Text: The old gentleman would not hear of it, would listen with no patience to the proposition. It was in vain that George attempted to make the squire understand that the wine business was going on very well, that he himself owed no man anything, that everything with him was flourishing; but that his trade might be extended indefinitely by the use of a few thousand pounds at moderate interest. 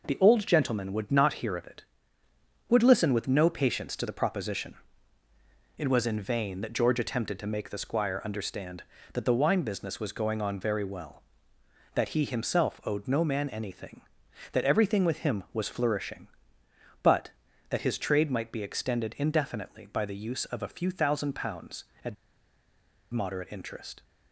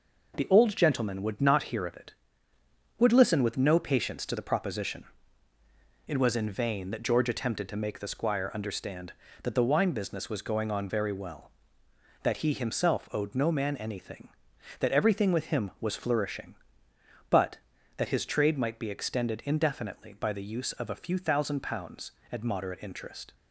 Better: second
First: pauses between "at" and "moderate"; noticeable; at 22.1 s; 0.96 s long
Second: none

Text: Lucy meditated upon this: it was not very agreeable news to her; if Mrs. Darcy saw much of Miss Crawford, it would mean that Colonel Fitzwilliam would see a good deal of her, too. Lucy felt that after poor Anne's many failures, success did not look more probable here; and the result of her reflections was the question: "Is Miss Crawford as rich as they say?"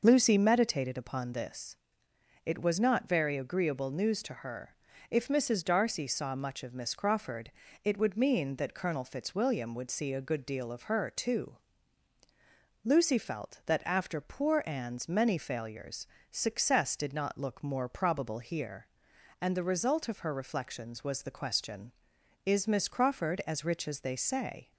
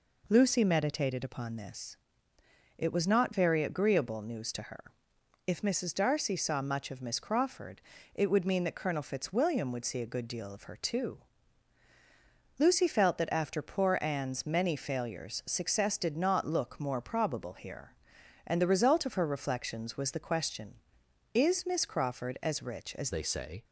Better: first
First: none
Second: changes voice at "they"; from 23.1 s on; 0.5 s long

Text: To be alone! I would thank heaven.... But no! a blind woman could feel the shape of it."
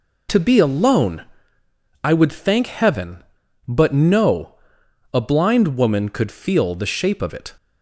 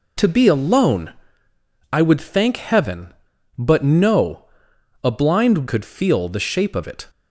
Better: first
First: none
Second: skips "woman"; at 5.6 s

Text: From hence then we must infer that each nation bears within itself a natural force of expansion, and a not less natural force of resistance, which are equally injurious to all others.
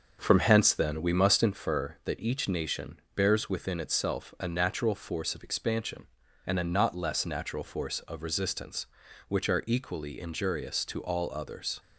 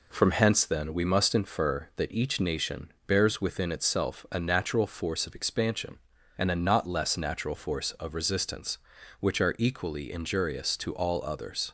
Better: second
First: starts louder than the rest; until 1.6 s; 6.5 dB // pauses between "nation" and "bears"; slight; at 2.9 s; 0.16 s long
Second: pauses between "nation" and "bears"; slight; at 2.9 s; 0.16 s long

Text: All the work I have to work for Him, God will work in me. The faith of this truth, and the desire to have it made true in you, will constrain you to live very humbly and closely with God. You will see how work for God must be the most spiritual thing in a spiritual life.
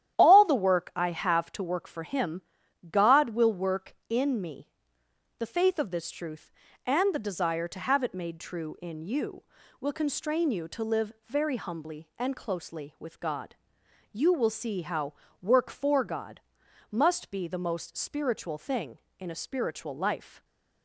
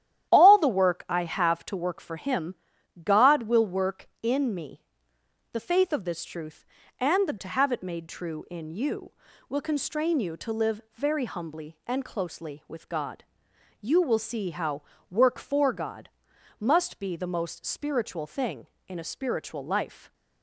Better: first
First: starts louder than the rest; strong; until 1.2 s; 11 dB // pauses between "how" and "work"; slight; at 15.1 s; 0.28 s long // pauses between "God" and "must"; noticeable; at 16.4 s; 0.52 s long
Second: starts louder than the rest; strong; until 1.3 s; 11.5 dB // skips "desire"; at 7.3 s // pauses between "how" and "work"; slight; at 14.8 s; 0.28 s long // pauses between "God" and "must"; noticeable; at 16.0 s; 0.52 s long

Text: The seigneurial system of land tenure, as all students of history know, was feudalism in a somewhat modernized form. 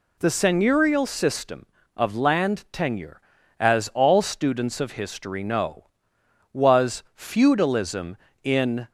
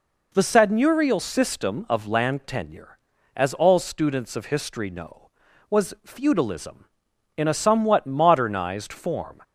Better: second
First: stops before "a somewhat modernized form"; at 8.8 s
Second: none

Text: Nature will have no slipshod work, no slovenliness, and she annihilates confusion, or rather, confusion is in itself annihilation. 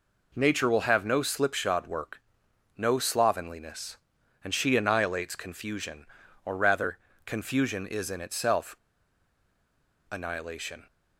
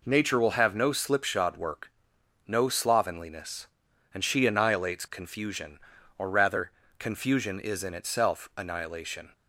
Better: second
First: pauses between "itself" and "annihilation"; strong; at 8.7 s; 1.3 s long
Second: none

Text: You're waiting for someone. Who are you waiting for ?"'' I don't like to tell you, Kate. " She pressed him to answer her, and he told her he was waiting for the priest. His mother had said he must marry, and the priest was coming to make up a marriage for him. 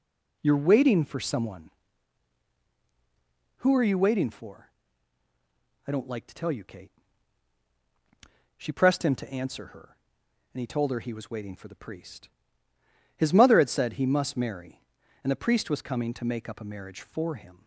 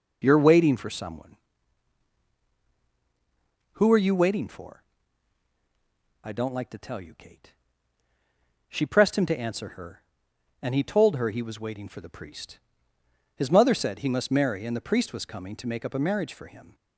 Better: first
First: starts louder than the rest; until 1.4 s; 6.5 dB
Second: starts louder than the rest; until 1.2 s; 6.5 dB // skips "had"; at 13.7 s

